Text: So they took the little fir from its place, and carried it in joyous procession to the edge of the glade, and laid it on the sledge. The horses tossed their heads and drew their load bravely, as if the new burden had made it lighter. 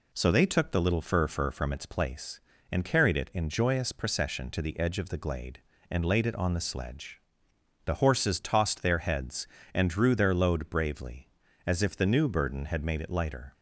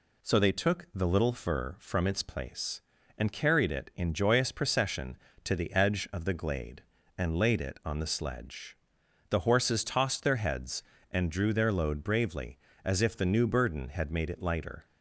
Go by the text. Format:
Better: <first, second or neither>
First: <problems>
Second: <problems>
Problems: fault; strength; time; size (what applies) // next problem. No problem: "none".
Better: second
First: says "fir" twice; at 1.2 s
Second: none